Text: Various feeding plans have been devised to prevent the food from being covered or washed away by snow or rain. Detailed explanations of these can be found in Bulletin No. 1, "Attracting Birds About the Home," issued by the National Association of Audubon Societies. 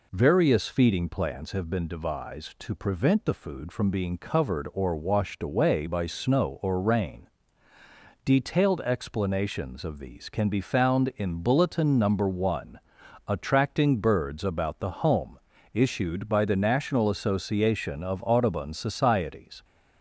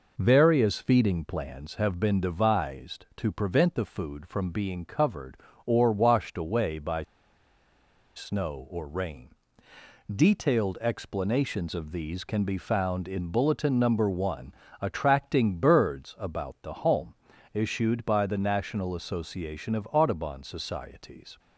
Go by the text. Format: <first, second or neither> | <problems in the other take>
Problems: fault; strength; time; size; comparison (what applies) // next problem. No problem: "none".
first | pauses between "by" and "snow"; at 7.0 s; 1.1 s long